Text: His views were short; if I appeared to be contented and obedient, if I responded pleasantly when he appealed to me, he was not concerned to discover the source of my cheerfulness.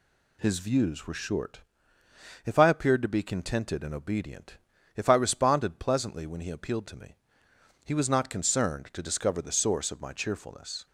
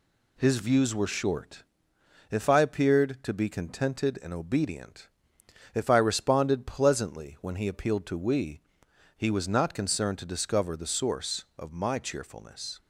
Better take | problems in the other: first | says "we" for "me"; at 8.1 s

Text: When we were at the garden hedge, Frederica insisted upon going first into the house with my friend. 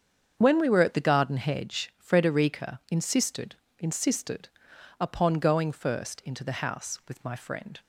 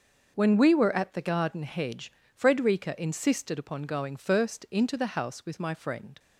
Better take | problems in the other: second | starts louder than the rest; strong; until 1.3 s; 7.5 dB; noticeable in the second // says "insisted" twice; at 3.7 s

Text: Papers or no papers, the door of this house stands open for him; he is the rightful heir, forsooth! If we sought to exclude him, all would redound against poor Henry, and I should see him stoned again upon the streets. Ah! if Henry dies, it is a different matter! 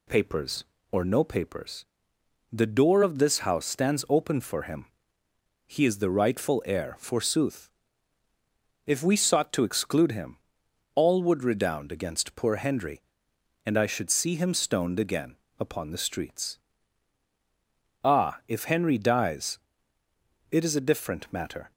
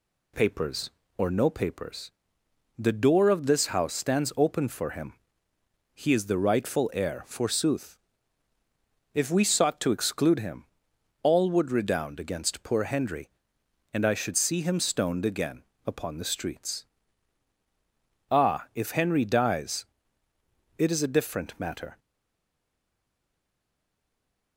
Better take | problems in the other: first | pauses between "again" and "upon"; slight; at 15.6 s; 0.20 s long; slight in the first // stays silent after the last word; strong; from 21.9 s on; 2.6 s long

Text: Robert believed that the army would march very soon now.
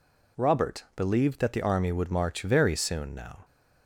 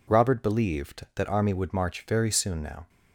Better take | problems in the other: first | skips "the"; at 1.2 s

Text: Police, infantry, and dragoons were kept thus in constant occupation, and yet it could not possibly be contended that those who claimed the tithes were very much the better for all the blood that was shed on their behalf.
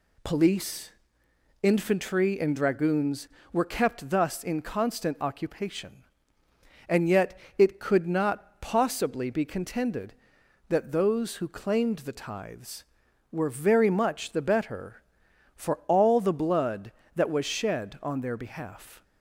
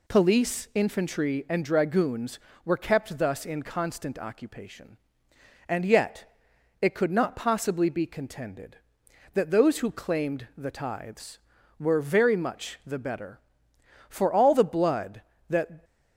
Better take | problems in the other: first | pauses between "yet" and "it"; noticeable; at 6.3 s; 0.48 s long; slight in the first // stops before "was shed on their behalf"; at 15.8 s

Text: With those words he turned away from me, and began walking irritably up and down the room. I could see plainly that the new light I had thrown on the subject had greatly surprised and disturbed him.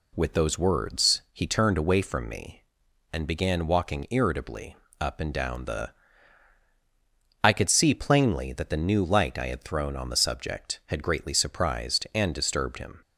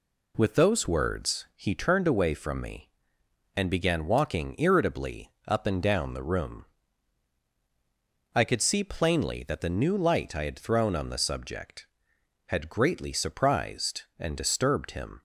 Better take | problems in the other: second | pauses between "irritably" and "up"; slight; at 4.7 s; 0.24 s long; slight in the second // skips "room"; at 6.6 s

